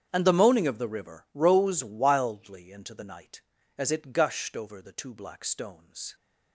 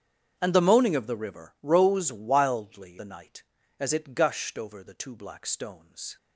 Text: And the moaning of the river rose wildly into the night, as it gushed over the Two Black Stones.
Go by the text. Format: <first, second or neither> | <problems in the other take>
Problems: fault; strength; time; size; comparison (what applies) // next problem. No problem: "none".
first | starts louder than the rest; strong; until 1.3 s; 7.5 dB; strong in the first // skips "into"; at 2.9 s